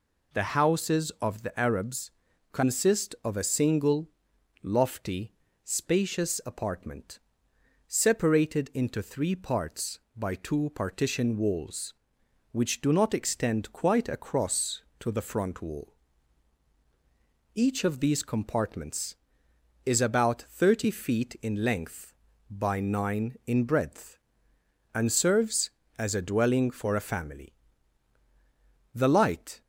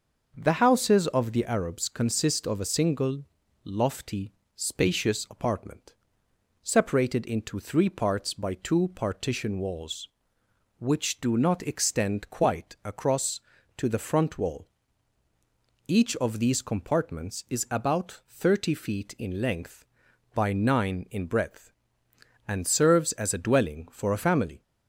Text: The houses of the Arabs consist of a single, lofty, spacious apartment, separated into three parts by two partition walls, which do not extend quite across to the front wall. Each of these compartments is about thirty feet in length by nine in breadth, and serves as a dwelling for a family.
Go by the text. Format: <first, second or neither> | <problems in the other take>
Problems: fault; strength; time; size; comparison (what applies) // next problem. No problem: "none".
second | pauses between "Arabs" and "consist"; at 2.1 s; 0.42 s long // goes on to say "The light"; noticeable; from 28.9 s on; 0.68 s long